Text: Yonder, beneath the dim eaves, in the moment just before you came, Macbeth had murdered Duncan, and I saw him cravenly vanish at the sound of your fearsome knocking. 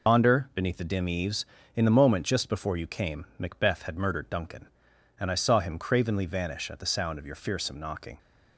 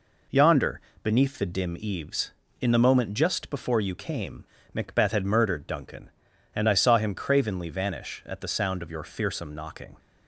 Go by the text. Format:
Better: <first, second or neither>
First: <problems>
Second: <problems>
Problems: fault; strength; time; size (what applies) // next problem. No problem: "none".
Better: second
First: loses the start of "Yonder"; at 0.0 s; 85 ms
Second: none